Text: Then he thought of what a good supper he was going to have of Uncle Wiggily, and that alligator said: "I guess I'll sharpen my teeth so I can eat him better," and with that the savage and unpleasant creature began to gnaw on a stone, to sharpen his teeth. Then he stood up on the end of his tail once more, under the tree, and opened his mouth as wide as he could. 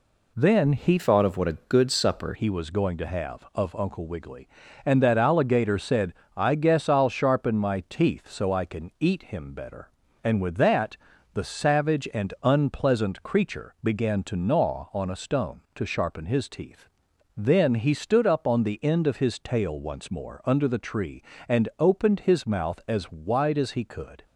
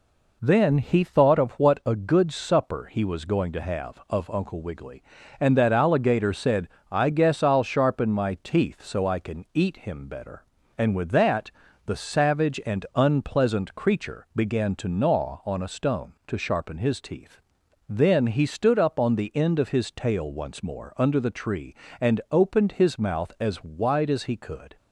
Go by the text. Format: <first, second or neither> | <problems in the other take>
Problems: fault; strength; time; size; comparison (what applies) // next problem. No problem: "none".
second | changes voice from "thought" to "supper"; from 0.9 to 2.3 s; 1.4 s long // pauses between "that" and "the"; at 10.9 s; 0.38 s long; slight in the second